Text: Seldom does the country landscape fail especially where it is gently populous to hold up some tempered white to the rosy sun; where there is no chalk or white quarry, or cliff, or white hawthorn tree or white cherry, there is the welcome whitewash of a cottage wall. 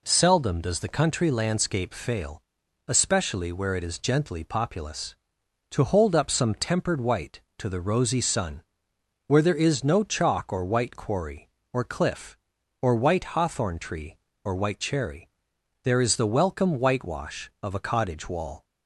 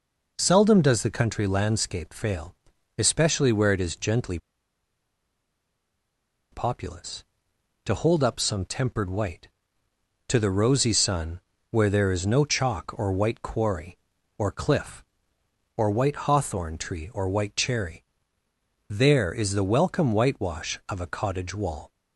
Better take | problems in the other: first | pauses between "fail" and "especially"; at 2.5 s; 0.44 s long; also in the first // pauses between "gently" and "populous"; strong; at 4.3 s; 2.1 s long

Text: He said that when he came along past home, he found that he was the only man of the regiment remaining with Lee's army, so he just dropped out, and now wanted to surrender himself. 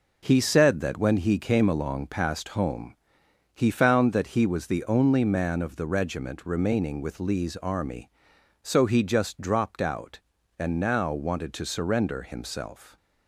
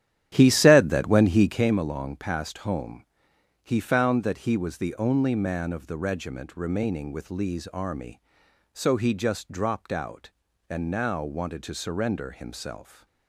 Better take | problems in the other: first | starts louder than the rest; strong; until 1.7 s; 11 dB

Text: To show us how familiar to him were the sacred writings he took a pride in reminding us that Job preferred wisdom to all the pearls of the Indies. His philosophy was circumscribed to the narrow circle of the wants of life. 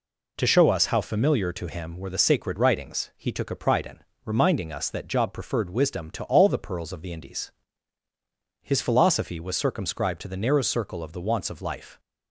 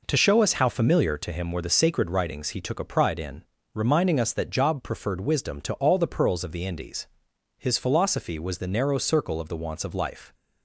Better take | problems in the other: first | pauses between "in" and "reminding"; slight; at 3.4 s; 0.30 s long; slight in the first // skips "circumscribed to"; at 8.5 s

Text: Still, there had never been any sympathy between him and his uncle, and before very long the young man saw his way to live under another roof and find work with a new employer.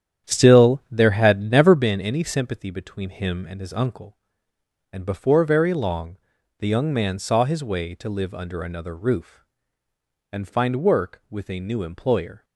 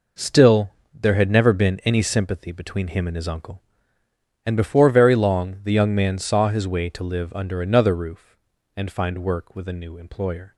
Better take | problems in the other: second | starts louder than the rest; strong; until 1.9 s; 9.5 dB // pauses between "long" and "the"; at 6.1 s; 0.42 s long

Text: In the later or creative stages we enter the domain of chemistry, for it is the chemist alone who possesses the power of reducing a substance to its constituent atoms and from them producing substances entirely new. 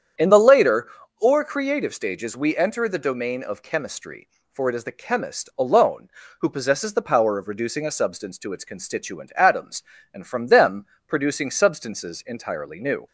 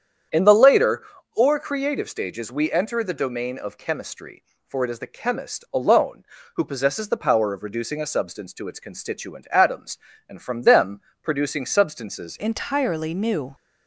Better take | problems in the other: first | starts louder than the rest; strong; until 1.6 s; 8.5 dB; strong in the first // pauses between "them" and "producing"; slight; at 10.9 s; 0.22 s long; slight in the first // changes voice at "entirely"; from 12.3 s on; 1.2 s long

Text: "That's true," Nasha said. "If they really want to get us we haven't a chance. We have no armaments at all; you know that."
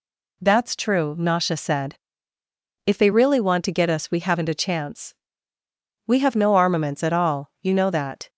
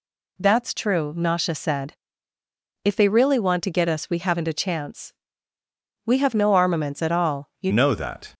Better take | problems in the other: first | changes voice at "know"; from 7.7 s on; 0.6 s long

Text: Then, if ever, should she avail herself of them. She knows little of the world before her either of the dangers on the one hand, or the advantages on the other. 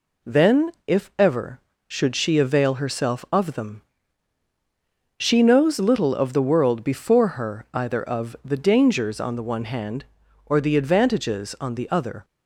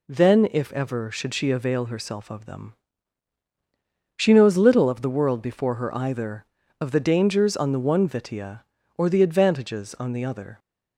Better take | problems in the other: first | says "vitia" for "hand"; at 8.0 s

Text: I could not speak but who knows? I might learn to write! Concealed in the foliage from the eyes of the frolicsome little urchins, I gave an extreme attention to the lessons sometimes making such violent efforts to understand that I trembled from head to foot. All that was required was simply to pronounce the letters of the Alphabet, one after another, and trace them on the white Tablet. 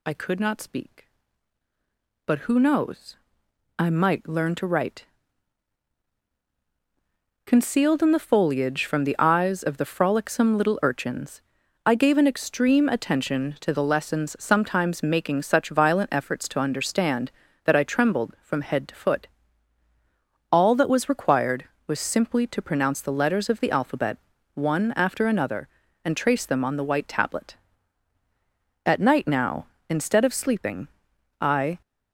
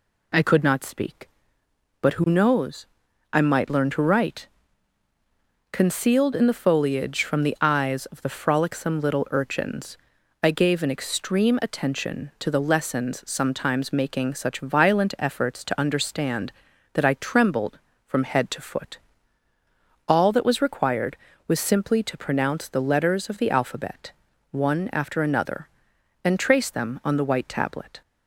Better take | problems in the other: second | goes on to say "At night now instead of sleeping I"; strong; from 28.8 s on; 2.9 s long

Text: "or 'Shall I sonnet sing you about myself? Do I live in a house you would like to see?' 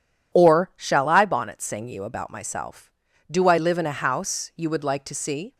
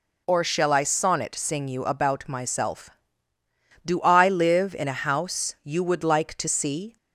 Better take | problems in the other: second | says "bonnet" for "sonnet"; at 1.2 s

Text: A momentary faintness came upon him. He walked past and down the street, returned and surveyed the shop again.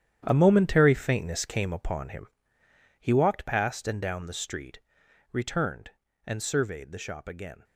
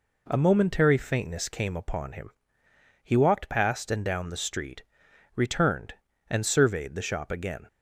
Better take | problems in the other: second | gets quieter; strong; throughout; 12 dB

